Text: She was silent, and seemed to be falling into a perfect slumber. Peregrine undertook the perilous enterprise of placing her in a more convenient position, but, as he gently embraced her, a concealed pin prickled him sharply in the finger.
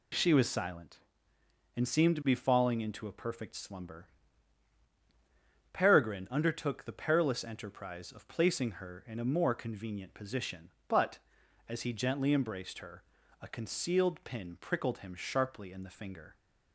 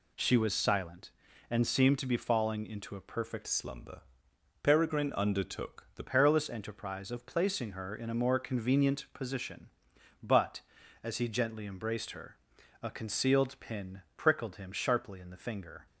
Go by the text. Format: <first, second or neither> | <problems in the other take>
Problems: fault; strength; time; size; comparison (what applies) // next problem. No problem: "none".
first | changes voice from "slumber" to "the"; from 3.4 to 6.0 s; 2.6 s long